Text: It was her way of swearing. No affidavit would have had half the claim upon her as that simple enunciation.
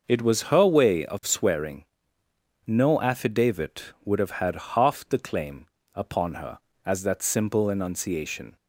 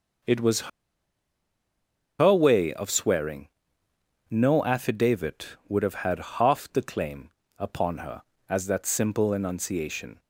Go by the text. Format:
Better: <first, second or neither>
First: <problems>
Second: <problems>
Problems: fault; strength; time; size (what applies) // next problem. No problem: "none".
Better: first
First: pauses between "claim" and "upon"; slight; at 5.6 s; 0.28 s long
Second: pauses between "was" and "her"; strong; at 0.6 s; 1.5 s long // pauses between "claim" and "upon"; slight; at 7.2 s; 0.28 s long